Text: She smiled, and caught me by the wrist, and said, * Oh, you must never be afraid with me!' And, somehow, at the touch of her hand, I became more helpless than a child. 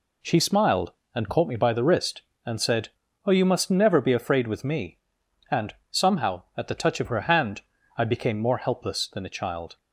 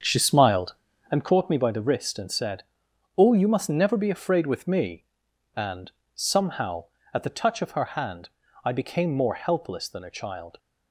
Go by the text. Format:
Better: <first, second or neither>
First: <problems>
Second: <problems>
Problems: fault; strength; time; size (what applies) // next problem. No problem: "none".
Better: first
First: none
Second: starts louder than the rest; strong; until 1.3 s; 7 dB